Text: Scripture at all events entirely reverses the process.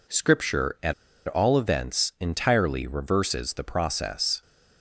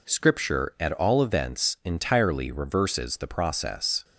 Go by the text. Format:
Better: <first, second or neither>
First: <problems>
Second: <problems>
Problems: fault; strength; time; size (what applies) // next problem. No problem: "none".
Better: second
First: pauses between "at" and "all"; slight; at 0.9 s; 0.33 s long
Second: none